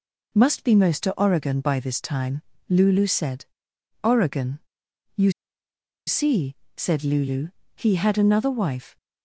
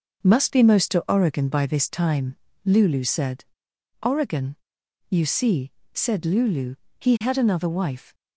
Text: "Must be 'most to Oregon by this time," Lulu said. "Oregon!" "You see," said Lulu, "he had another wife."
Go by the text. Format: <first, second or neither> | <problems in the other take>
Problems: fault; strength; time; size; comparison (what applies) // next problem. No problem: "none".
second | pauses between "You" and "see"; noticeable; at 5.3 s; 0.75 s long